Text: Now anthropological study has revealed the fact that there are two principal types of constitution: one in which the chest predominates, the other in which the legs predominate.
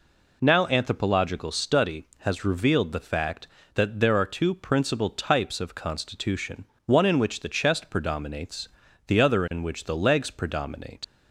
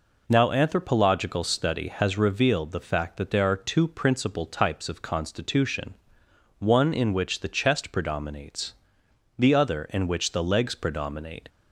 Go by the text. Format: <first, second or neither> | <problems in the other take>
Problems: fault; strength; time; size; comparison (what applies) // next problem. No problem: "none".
second | leaves "predominate" unfinished; at 11.0 s; 60 ms